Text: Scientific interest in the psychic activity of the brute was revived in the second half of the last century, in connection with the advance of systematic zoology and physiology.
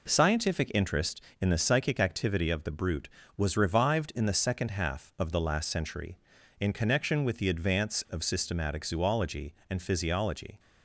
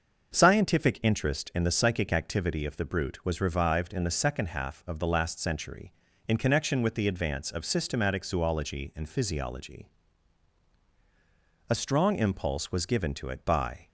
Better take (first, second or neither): first